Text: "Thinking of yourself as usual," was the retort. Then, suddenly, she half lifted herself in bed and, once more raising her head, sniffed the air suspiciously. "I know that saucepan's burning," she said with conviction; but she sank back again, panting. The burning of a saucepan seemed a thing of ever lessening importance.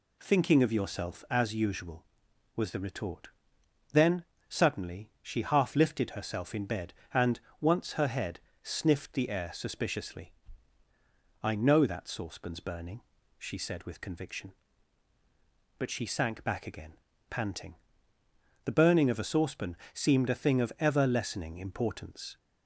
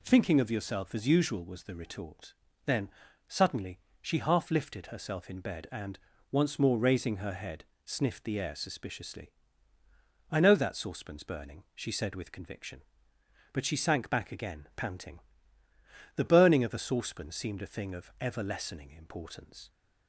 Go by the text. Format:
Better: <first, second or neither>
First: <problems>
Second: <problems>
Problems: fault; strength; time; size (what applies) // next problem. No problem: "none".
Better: second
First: skips "more raising"; at 7.9 s // pauses between "saucepan" and "seemed"; slight; at 19.7 s; 0.16 s long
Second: none